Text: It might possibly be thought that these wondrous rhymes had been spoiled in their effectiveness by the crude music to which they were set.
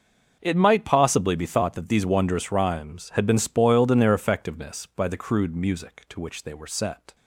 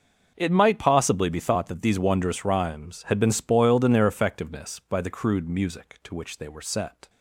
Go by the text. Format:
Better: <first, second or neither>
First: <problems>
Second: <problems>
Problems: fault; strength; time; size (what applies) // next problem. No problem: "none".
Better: neither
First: starts louder than the rest; until 1.4 s; 6.5 dB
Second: starts louder than the rest; until 1.3 s; 6.5 dB